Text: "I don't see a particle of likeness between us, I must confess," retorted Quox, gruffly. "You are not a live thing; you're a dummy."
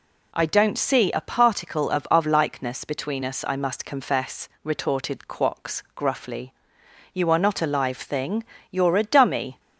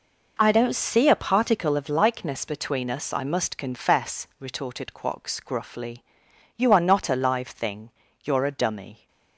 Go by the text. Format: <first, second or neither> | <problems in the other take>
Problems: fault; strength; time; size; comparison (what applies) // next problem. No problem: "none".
second | says "of" twice; at 2.1 s